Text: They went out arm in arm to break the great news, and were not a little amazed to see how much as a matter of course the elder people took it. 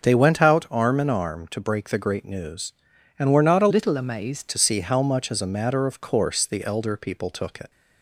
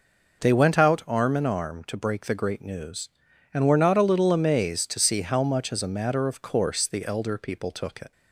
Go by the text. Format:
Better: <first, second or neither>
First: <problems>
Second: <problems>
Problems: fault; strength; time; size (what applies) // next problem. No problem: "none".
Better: second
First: starts louder than the rest; until 1.0 s; 6.5 dB // changes voice from "little" to "amazed"; from 3.6 to 4.4 s; 0.8 s long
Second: none